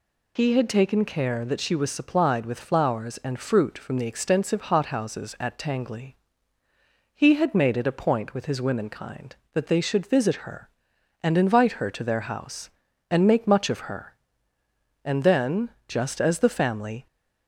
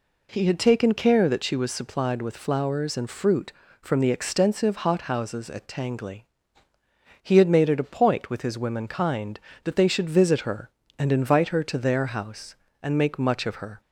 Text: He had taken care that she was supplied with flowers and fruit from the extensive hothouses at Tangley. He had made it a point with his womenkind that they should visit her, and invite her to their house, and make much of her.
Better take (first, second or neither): second